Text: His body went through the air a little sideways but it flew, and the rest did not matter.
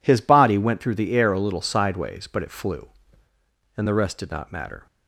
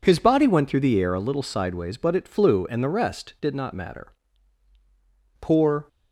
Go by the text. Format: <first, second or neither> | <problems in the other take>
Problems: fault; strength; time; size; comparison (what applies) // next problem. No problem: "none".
first | goes on to say "Poor"; slight; from 5.3 s on; 0.48 s long